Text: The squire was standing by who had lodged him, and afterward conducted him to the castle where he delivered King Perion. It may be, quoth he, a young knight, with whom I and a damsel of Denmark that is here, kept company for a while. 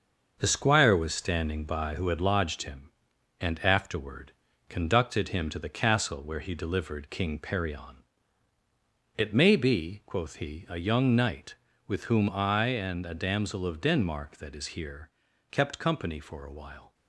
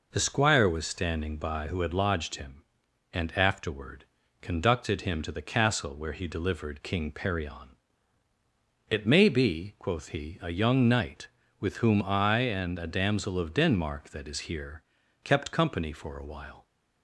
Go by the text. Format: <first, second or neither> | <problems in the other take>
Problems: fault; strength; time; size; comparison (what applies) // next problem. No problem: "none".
second | gets quieter; throughout; 6.5 dB // pauses between "afterward" and "conducted"; at 4.2 s; 0.38 s long; also in the second